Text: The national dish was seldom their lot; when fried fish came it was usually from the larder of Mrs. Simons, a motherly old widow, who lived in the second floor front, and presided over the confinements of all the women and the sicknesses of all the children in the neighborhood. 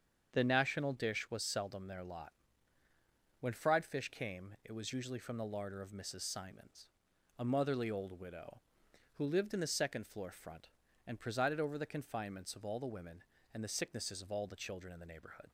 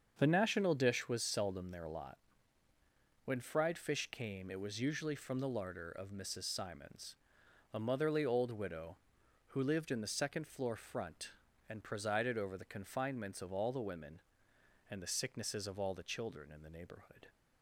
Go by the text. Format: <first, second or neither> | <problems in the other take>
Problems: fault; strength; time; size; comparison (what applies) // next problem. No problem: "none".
neither | starts louder than the rest; the same in both